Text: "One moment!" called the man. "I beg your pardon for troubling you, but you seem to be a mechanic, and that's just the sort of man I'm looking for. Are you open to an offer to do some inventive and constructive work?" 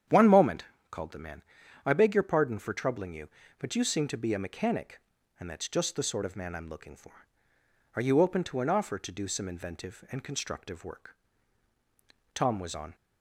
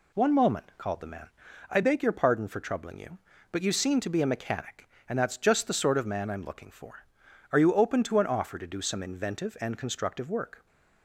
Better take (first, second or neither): second